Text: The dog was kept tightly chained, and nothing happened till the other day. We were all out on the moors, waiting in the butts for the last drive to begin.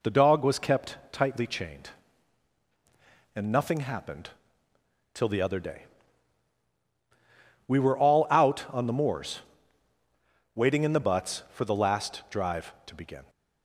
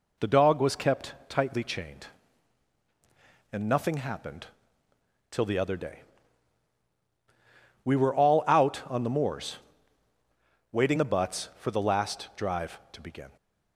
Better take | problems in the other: first | pauses between "happened" and "till"; noticeable; at 4.4 s; 0.82 s long; noticeable in the first // skips "in"; at 10.9 s

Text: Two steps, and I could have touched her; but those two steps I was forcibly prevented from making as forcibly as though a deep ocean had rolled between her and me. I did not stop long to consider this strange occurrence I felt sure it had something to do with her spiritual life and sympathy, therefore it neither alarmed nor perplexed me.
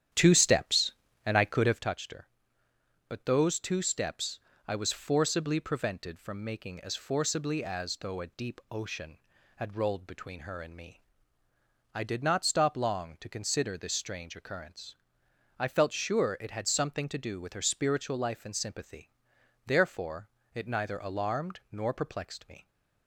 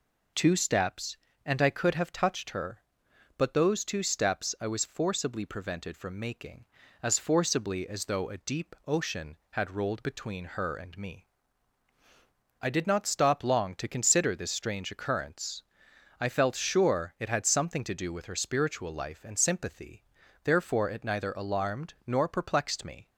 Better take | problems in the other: second | starts louder than the rest; strong; until 1.9 s; 10 dB // pauses between "steps" and "I"; slight; at 4.4 s; 0.26 s long // pauses between "occurrence" and "I"; noticeable; at 14.9 s; 0.66 s long; noticeable in the second // pauses between "therefore" and "it"; slight; at 20.2 s; 0.26 s long

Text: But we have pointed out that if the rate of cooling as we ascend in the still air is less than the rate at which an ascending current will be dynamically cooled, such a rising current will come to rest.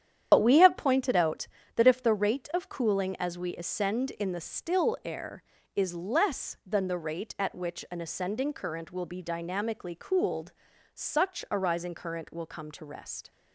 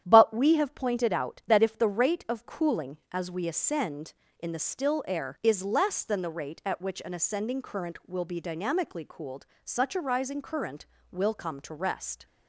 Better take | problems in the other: second | loses the start of "But"; at 0.3 s; 45 ms // starts louder than the rest; strong; until 1.3 s; 9.5 dB; strong in the second

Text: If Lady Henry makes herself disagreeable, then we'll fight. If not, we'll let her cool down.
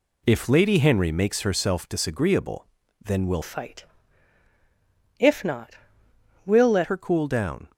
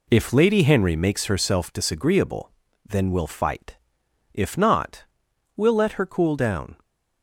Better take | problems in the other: second | changes voice from "fight" to "let"; from 3.4 to 6.8 s; 3.4 s long

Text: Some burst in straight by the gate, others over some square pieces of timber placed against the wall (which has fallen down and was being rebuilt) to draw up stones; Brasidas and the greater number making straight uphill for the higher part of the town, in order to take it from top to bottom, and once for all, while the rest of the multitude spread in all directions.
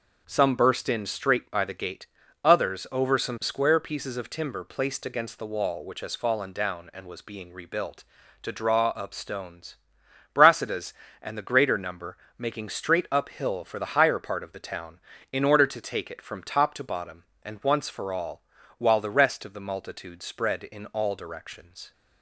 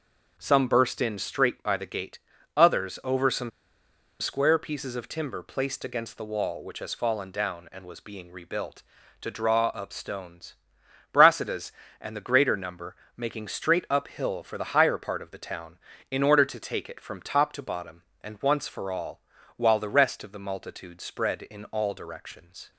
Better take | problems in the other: first | pauses between "some" and "square"; noticeable; at 3.5 s; 0.70 s long // pauses between "number" and "making"; slight; at 12.9 s; 0.22 s long; slight in the first

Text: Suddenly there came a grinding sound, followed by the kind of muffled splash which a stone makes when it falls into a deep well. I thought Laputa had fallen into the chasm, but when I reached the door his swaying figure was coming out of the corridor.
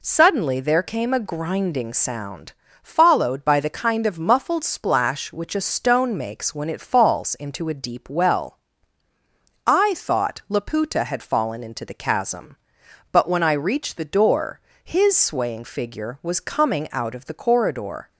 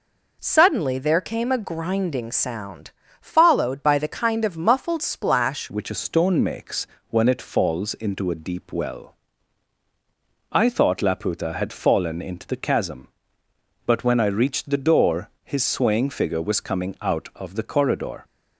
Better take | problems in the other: first | changes voice at "which"; from 5.6 s on; 12.6 s long // pauses between "makes" and "when"; slight; at 6.8 s; 0.24 s long // pauses between "door" and "his"; slight; at 15.2 s; 0.16 s long; slight in the first

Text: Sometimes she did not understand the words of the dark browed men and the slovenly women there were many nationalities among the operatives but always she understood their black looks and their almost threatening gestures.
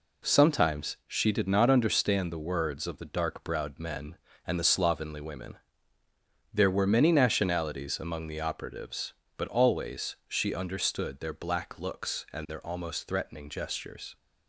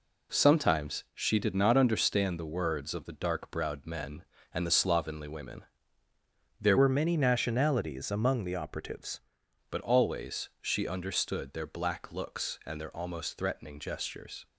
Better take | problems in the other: first | pauses between "women" and "there"; noticeable; at 5.6 s; 0.98 s long; noticeable in the first // changes voice from "were" to "operatives"; from 6.7 to 9.1 s; 2.4 s long

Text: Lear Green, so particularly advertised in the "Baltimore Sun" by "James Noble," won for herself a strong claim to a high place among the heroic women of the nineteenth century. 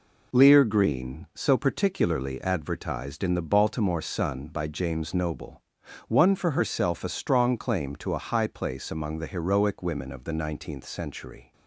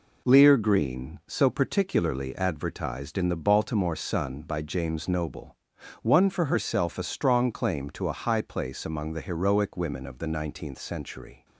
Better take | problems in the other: neither | none

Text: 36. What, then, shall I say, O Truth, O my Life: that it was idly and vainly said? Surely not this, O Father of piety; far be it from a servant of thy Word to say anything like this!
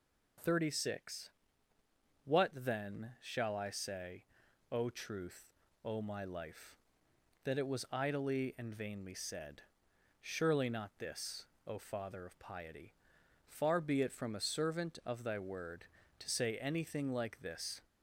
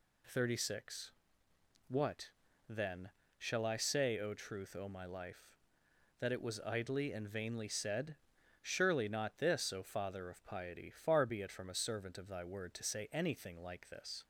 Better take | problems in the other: neither | none

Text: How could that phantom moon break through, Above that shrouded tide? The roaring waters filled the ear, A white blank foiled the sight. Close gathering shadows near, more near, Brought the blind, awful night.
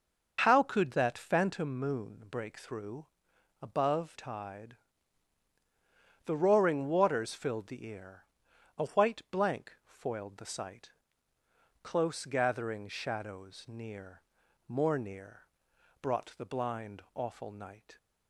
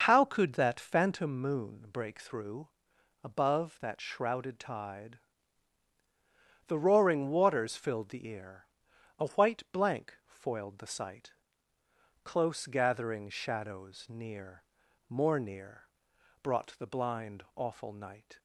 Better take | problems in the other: second | skips "that shrouded"; at 4.1 s

